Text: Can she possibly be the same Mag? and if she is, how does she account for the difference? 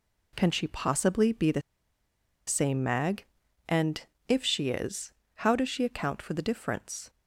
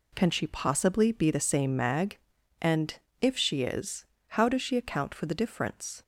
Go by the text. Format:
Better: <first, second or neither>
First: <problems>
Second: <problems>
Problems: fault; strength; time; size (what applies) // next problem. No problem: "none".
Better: second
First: pauses between "the" and "same"; noticeable; at 1.6 s; 0.86 s long // pauses between "and" and "if"; slight; at 4.0 s; 0.22 s long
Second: pauses between "and" and "if"; slight; at 2.9 s; 0.22 s long